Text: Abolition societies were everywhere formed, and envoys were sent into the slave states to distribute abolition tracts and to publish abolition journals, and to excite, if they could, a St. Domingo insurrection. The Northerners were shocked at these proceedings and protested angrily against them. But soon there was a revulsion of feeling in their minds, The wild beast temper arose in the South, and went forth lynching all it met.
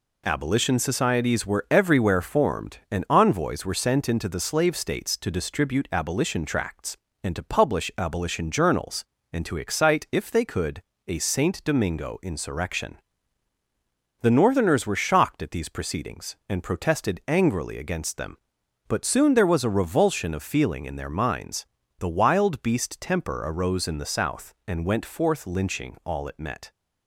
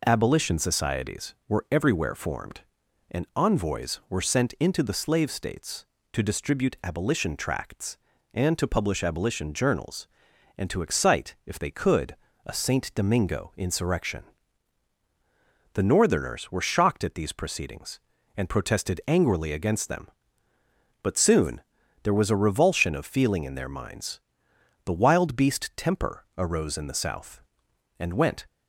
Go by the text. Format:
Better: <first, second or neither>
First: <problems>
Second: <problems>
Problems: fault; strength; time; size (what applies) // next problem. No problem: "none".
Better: first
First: none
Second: pauses between "soon" and "there"; at 21.6 s; 0.40 s long // stops before "forth lynching all it met"; at 28.4 s